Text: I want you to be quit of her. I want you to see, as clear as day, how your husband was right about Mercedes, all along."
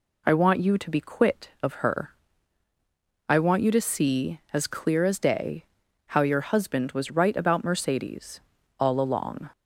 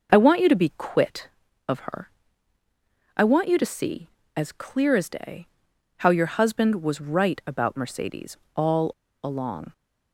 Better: first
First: none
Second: pauses between "all" and "along"; slight; at 8.9 s; 0.32 s long

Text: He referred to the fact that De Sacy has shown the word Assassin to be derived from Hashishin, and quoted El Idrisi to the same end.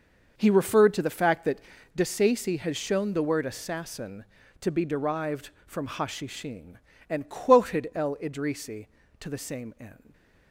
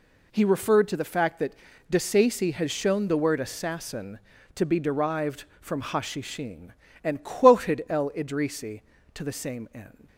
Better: second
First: starts louder than the rest; noticeable; until 2.0 s; 6 dB // pauses between "that" and "De"; slight; at 1.6 s; 0.34 s long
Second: pauses between "that" and "De"; slight; at 1.5 s; 0.34 s long

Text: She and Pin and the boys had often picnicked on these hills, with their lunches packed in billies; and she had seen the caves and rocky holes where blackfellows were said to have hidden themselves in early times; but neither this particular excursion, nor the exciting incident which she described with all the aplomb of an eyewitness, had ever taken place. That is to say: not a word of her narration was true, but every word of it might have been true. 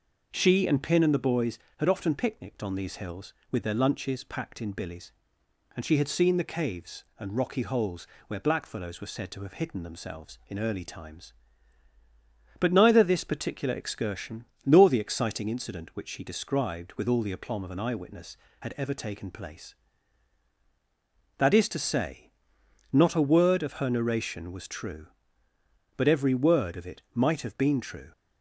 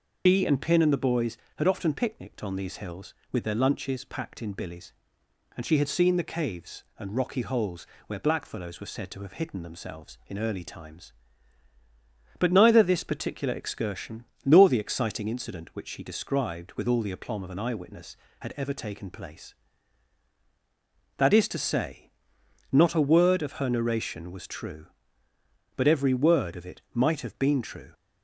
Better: first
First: pauses between "holes" and "where"; slight; at 8.0 s; 0.22 s long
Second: loses the start of "She"; at 0.2 s; 150 ms // pauses between "holes" and "where"; slight; at 7.8 s; 0.22 s long

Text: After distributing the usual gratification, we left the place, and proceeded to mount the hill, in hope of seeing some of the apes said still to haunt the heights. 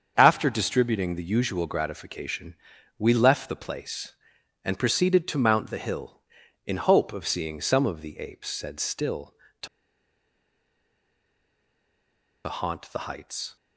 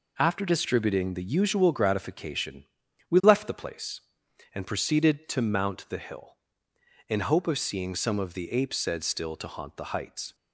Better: second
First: starts louder than the rest; until 1.1 s; 7 dB // pauses between "to" and "haunt"; strong; at 9.6 s; 2.7 s long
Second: none

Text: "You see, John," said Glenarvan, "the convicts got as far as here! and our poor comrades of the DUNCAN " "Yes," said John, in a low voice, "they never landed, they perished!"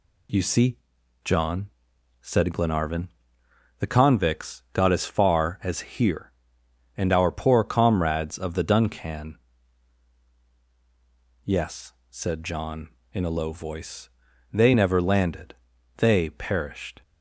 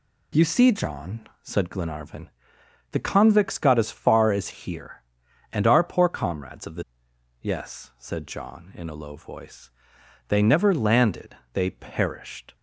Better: first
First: none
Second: skips "DUNCAN"; at 6.9 s

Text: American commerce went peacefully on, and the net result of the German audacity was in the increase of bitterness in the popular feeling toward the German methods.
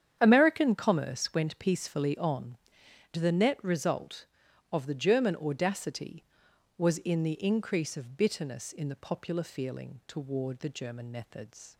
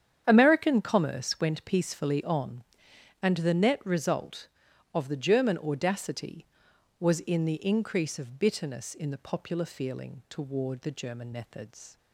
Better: second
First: starts louder than the rest; strong; until 1.2 s; 8.5 dB // skips "and"; at 2.8 s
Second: starts louder than the rest; strong; until 1.2 s; 8.5 dB

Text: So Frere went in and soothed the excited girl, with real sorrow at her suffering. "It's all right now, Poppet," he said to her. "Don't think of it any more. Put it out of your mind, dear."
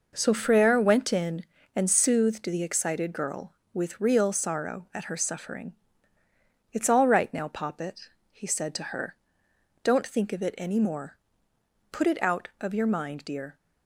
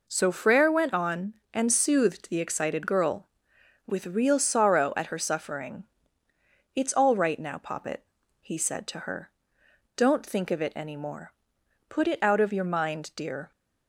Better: first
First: none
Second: says "on" for "in"; at 0.9 s

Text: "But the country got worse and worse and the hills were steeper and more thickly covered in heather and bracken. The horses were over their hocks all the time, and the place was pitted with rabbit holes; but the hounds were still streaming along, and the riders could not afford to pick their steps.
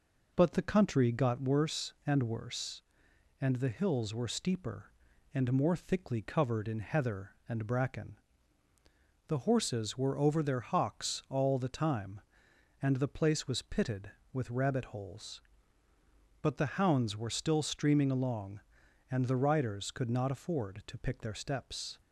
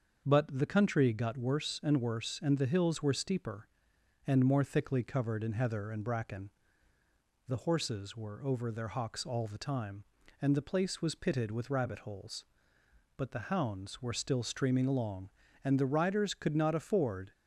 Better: first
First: none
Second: starts louder than the rest; until 1.2 s; 6.5 dB // stops before "to pick their steps"; at 17.3 s

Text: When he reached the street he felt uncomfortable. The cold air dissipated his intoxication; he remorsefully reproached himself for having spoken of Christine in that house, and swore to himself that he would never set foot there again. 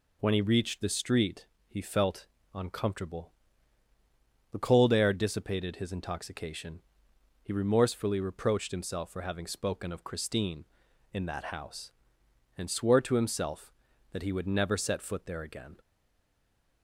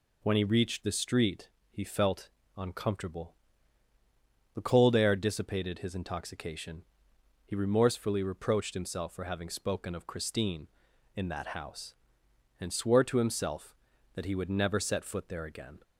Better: second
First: pauses between "street" and "he"; slight; at 1.4 s; 0.24 s long // pauses between "felt" and "uncomfortable"; slight; at 2.2 s; 0.28 s long // stays silent after the last word; from 15.7 s on; 1.1 s long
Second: pauses between "street" and "he"; slight; at 1.4 s; 0.24 s long // pauses between "felt" and "uncomfortable"; slight; at 2.2 s; 0.28 s long

